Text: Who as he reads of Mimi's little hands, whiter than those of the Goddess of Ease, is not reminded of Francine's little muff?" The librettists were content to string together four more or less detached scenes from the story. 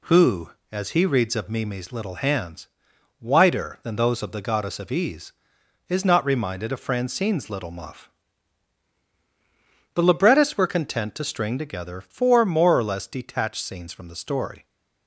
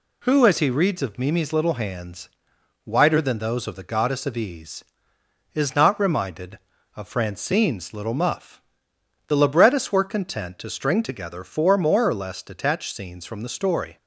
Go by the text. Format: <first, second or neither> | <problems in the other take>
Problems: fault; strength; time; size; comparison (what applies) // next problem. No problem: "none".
neither | none